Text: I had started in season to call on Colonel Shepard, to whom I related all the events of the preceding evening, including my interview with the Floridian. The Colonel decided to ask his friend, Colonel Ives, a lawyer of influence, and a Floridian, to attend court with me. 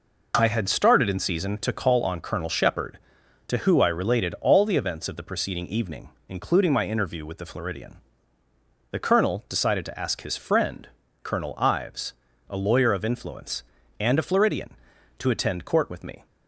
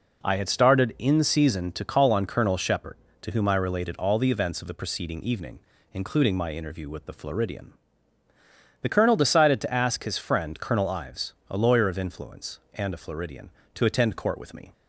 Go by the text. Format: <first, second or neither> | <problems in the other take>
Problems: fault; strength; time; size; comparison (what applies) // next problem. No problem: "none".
second | says "who" for "whom"; at 3.5 s